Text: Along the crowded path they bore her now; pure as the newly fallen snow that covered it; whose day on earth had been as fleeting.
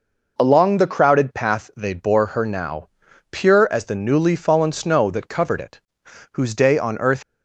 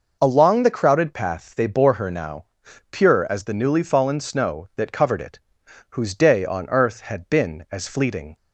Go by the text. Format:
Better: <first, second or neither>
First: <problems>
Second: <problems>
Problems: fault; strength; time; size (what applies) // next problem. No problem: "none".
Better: second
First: stops before "had been as fleeting"; at 7.2 s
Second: none